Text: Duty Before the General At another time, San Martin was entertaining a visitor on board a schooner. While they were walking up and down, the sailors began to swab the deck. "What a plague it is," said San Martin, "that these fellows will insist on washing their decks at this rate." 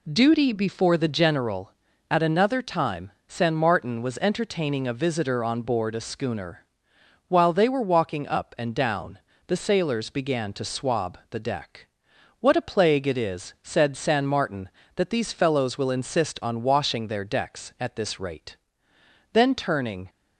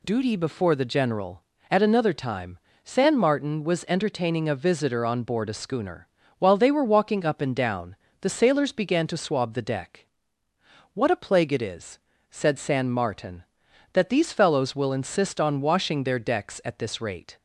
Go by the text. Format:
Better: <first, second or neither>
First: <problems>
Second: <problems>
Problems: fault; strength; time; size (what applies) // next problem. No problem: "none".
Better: second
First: goes on to say "Then turning"; noticeable; from 19.3 s on; 0.76 s long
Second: none